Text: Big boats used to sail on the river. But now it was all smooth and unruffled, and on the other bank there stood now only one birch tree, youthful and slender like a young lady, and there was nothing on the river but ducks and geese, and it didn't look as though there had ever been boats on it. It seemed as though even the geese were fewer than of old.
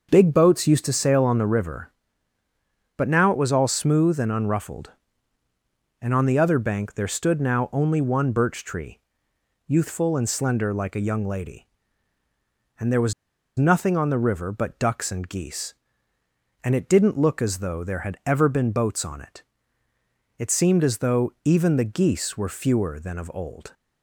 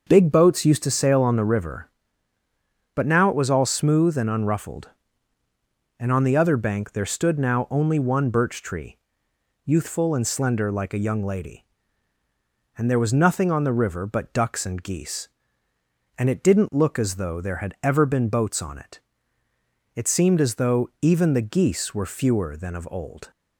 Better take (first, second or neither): second